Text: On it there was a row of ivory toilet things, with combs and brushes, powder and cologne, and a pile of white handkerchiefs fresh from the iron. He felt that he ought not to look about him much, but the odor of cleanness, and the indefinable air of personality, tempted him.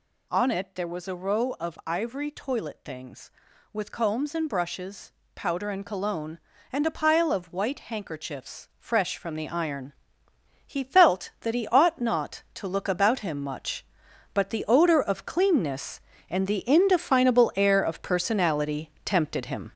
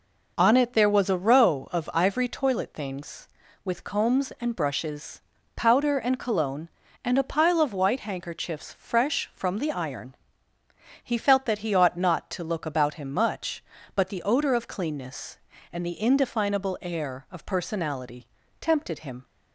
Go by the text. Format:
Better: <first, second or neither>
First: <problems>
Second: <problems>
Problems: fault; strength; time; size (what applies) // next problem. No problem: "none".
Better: second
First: gets louder; noticeable; throughout; 6 dB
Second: none